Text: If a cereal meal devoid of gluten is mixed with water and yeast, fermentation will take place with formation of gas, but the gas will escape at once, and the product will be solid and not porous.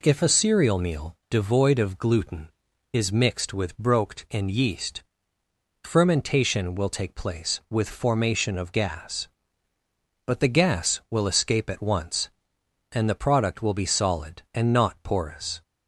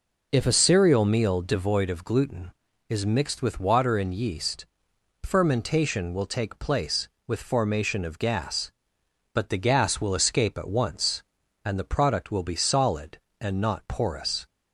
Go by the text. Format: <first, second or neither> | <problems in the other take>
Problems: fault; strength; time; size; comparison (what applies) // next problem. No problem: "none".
second | says "broked" for "water"; at 3.7 s